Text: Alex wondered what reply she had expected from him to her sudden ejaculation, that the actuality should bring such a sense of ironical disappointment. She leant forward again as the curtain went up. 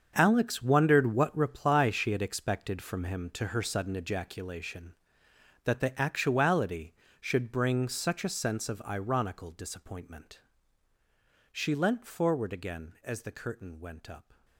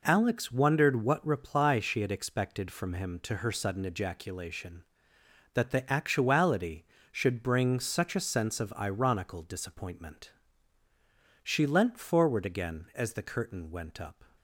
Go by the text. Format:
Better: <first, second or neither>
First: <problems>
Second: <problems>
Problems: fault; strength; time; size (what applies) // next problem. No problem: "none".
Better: second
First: gets quieter; strong; throughout; 13 dB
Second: none